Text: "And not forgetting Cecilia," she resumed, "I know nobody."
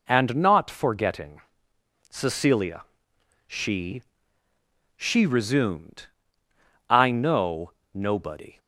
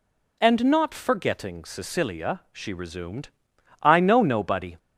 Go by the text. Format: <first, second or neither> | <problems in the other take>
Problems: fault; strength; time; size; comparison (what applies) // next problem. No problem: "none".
second | pauses between "forgetting" and "Cecilia"; noticeable; at 1.4 s; 0.68 s long // says "she" twice; at 4.9 s // pauses between "know" and "nobody"; slight; at 7.7 s; 0.22 s long